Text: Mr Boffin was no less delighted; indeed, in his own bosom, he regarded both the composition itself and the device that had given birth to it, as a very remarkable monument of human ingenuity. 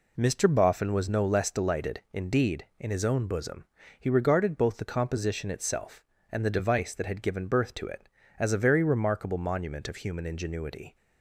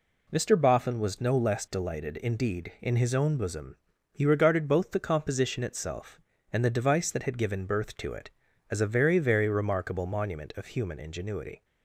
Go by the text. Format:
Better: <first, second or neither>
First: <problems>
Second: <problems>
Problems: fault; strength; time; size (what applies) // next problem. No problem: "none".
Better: first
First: none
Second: says "very" twice; at 9.1 s